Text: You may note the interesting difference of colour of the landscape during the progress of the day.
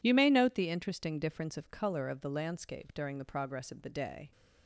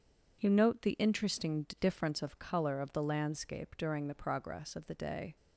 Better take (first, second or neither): first